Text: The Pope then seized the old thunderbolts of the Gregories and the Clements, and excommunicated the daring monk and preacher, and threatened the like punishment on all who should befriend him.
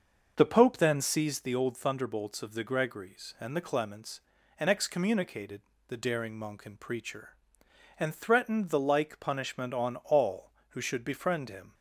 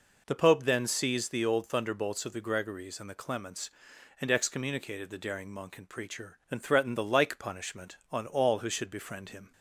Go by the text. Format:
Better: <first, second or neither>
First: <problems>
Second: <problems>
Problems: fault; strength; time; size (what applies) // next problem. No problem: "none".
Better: second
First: starts louder than the rest; until 1.6 s; 6.5 dB // pauses between "excommunicated" and "the"; slight; at 5.6 s; 0.26 s long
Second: none